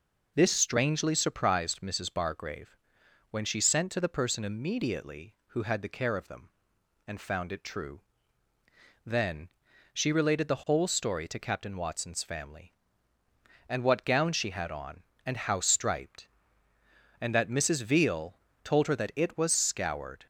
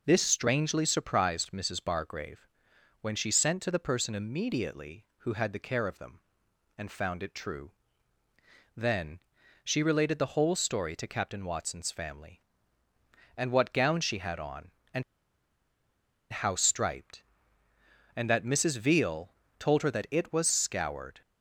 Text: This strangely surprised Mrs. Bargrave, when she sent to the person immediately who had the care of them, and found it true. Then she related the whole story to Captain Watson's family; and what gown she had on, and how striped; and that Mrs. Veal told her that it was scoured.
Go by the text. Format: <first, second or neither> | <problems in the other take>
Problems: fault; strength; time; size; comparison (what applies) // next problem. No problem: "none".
first | pauses between "Then" and "she"; at 9.2 s; 0.44 s long; also in the first // pauses between "and" and "how"; strong; at 15.0 s; 1.2 s long // pauses between "Veal" and "told"; slight; at 19.3 s; 0.24 s long; slight in the first